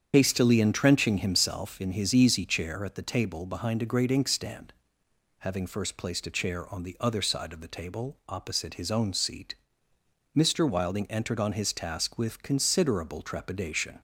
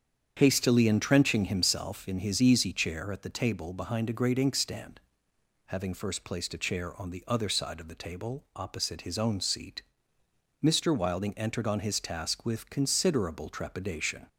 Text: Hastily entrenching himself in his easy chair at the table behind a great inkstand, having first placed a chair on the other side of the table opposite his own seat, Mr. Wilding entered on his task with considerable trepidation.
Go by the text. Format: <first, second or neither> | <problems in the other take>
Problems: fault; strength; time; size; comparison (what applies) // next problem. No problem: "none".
second | loses the start of "Hastily"; at 0.1 s; 45 ms // starts louder than the rest; strong; until 1.1 s; 8 dB; strong in the second